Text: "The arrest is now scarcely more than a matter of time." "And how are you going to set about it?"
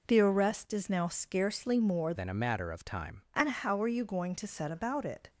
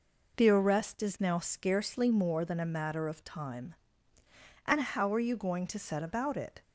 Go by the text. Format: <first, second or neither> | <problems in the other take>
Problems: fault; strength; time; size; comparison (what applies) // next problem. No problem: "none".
second | changes voice from "than" to "time"; from 2.1 to 3.2 s; 1.1 s long